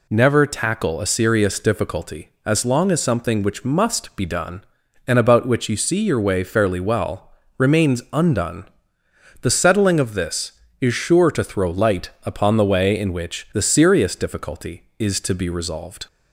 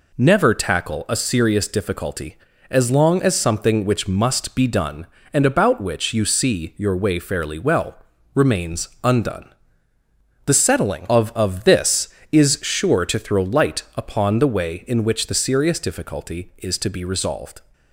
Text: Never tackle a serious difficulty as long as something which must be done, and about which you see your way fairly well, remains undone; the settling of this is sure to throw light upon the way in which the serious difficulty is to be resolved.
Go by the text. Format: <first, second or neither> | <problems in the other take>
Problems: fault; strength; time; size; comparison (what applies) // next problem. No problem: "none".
first | pauses between "remains" and "undone"; slight; at 8.8 s; 0.16 s long // says "of" twice; at 11.3 s